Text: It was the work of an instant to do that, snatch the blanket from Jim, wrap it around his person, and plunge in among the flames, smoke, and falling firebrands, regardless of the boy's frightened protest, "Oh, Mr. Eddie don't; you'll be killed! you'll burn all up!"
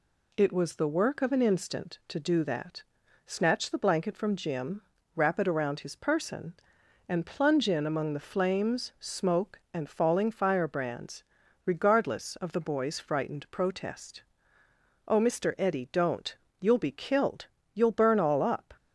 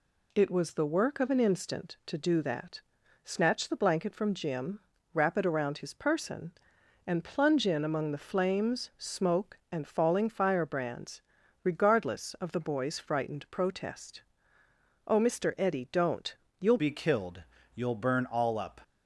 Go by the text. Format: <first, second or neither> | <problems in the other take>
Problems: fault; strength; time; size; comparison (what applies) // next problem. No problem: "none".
first | changes voice at "be"; from 16.7 s on; 2.0 s long